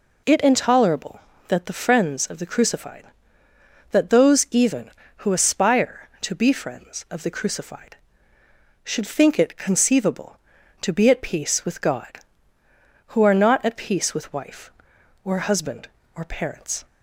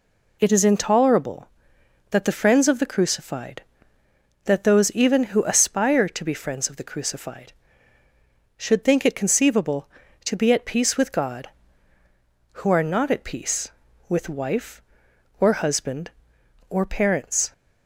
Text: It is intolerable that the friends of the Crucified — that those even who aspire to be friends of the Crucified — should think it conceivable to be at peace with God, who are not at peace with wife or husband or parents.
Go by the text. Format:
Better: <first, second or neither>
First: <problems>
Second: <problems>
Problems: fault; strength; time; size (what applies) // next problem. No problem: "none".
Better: second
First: skips "is"; at 0.3 s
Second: none